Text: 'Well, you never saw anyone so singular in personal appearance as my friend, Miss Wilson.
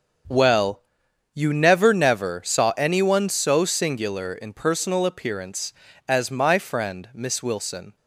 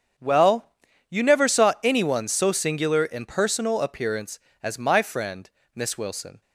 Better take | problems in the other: second | starts louder than the rest; until 1.8 s; 6.5 dB; also in the second // says "never" twice; at 1.9 s

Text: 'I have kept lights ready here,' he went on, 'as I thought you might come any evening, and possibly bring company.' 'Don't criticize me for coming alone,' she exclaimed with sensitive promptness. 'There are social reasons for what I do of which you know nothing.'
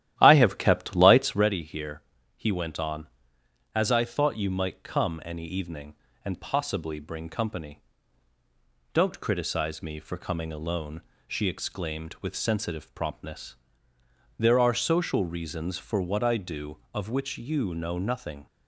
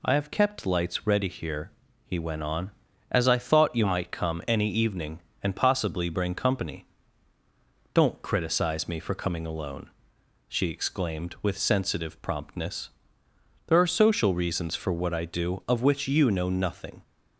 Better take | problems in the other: second | starts louder than the rest; strong; until 1.5 s; 12.5 dB

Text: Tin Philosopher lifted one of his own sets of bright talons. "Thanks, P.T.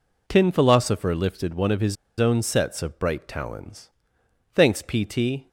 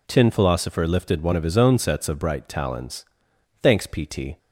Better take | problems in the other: second | pauses between "his" and "own"; slight; at 1.9 s; 0.24 s long

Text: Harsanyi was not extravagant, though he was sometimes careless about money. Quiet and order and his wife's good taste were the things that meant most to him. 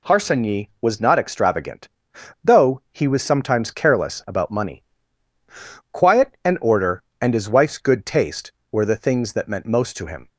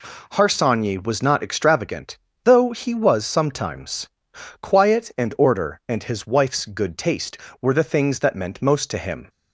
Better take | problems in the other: first | skips "careless about money"; at 4.3 s

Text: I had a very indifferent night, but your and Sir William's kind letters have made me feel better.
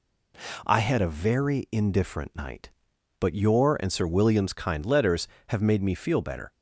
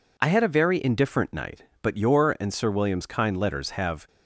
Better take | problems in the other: first | stops before "made me feel better"; at 4.0 s

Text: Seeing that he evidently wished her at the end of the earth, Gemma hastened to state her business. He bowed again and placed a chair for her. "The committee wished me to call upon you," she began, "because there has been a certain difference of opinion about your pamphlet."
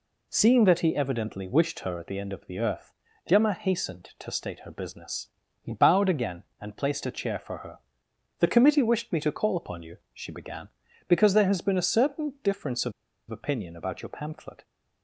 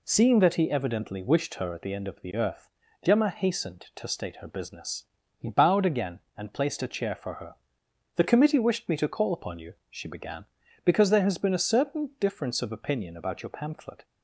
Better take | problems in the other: second | pauses between "of" and "opinion"; at 12.9 s; 0.37 s long

